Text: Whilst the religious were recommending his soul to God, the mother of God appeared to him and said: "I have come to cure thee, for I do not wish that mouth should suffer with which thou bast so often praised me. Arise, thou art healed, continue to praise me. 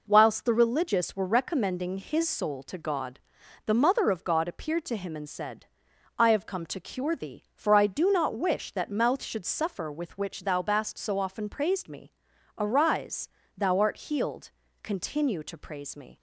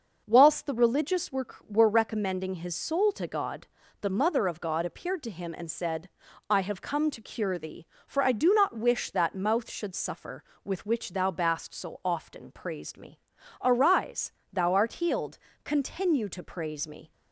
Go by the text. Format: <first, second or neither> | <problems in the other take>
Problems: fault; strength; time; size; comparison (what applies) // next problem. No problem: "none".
first | says "were" twice; at 1.6 s